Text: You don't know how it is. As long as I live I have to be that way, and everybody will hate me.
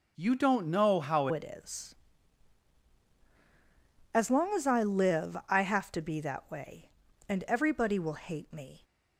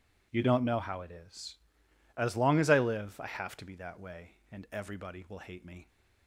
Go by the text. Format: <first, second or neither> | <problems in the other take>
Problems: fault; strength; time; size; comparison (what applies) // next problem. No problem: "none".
second | changes voice at "it"; from 1.3 s on; 7.5 s long